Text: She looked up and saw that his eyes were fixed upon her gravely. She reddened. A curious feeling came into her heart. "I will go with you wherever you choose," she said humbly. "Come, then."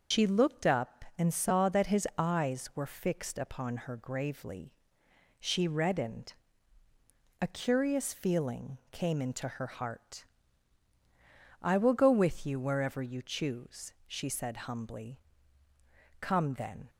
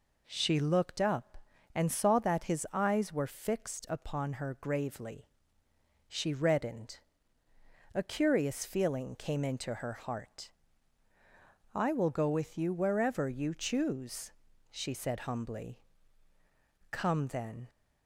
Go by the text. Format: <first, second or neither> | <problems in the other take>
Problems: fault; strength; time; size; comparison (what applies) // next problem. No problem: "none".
second | loses the start of "She"; at 0.1 s; 100 ms // starts louder than the rest; until 1.2 s; 6.5 dB